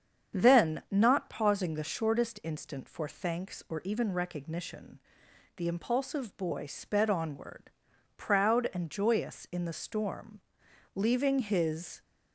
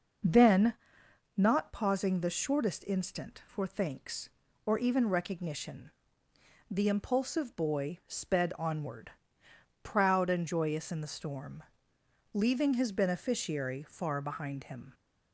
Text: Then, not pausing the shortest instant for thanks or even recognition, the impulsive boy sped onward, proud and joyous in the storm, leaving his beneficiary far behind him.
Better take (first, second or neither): second